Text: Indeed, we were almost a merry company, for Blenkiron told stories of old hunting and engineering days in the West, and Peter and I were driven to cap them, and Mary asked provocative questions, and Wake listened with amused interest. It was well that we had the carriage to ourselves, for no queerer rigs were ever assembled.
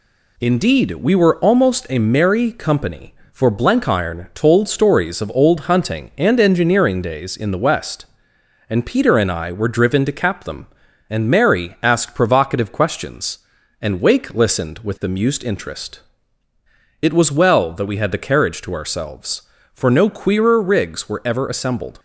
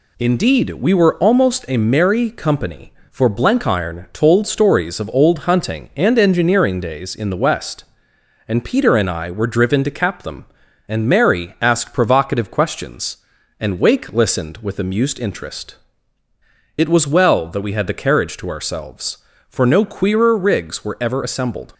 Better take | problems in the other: neither | none

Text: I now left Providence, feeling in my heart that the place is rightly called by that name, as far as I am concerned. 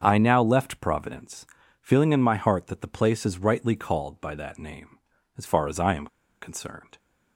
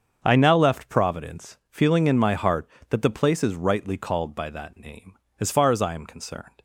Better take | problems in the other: second | starts louder than the rest; until 1.0 s; 7 dB; also in the second // pauses between "am" and "concerned"; slight; at 6.0 s; 0.33 s long

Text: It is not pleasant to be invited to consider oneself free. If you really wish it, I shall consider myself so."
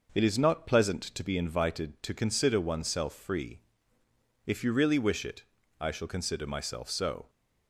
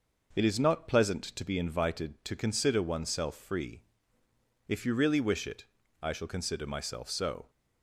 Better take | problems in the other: neither | none

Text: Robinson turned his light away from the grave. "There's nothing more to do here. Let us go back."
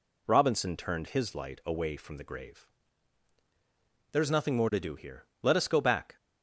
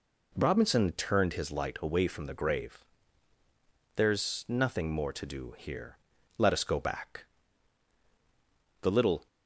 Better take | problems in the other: first | goes on to say "The little"; slight; from 8.8 s on; 0.46 s long

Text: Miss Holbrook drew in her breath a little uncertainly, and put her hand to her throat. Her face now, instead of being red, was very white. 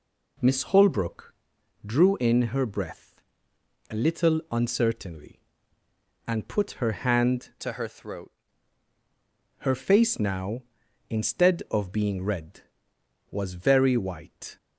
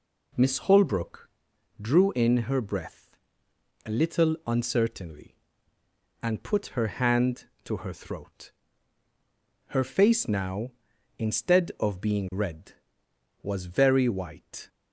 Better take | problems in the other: second | pauses between "Holbrook" and "drew"; noticeable; at 1.3 s; 0.50 s long; noticeable in the second // pauses between "breath" and "a"; noticeable; at 3.1 s; 0.74 s long; noticeable in the second // changes voice from "to" to "throat"; from 7.6 to 8.3 s; 0.7 s long

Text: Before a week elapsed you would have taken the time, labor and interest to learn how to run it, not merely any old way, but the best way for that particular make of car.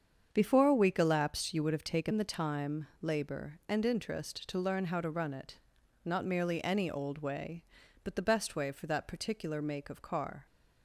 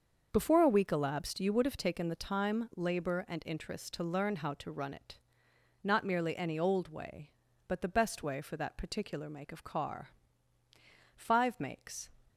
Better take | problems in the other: first | starts louder than the rest; until 1.3 s; 6.5 dB; strong in the first // goes on to say "Five Makes"; noticeable; from 11.1 s on; 0.94 s long

